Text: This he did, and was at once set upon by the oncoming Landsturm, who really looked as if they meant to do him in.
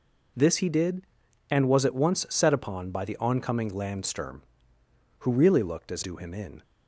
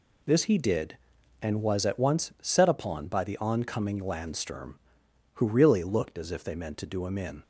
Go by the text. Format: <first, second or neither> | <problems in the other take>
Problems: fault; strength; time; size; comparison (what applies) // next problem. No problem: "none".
second | skips "if they meant to"; at 6.0 s